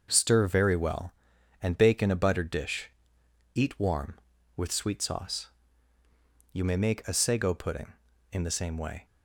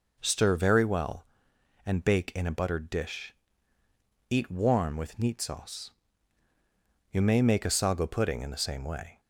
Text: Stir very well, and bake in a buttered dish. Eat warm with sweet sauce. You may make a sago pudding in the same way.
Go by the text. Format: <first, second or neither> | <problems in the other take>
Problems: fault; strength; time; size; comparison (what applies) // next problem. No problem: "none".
first | says "neat" for "sweet"; at 5.1 s